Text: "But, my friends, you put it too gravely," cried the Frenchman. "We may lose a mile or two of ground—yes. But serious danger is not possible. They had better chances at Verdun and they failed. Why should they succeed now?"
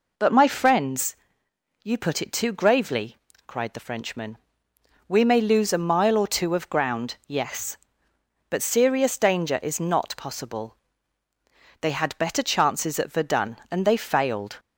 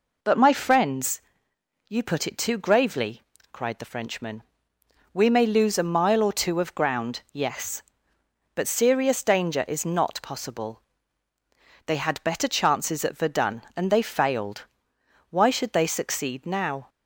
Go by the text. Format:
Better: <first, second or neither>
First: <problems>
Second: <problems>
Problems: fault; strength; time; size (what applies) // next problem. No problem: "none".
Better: second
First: stops before "Why should they succeed now"; at 14.5 s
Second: none